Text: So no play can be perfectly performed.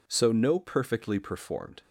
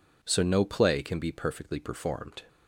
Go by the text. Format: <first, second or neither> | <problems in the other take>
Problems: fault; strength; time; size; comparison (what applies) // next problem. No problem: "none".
second | skips "play can be"; at 0.5 s